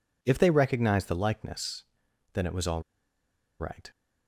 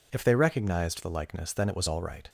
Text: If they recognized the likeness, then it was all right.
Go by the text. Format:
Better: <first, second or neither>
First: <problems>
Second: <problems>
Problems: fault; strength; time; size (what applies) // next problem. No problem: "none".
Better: second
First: pauses between "all" and "right"; noticeable; at 2.8 s; 0.77 s long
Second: none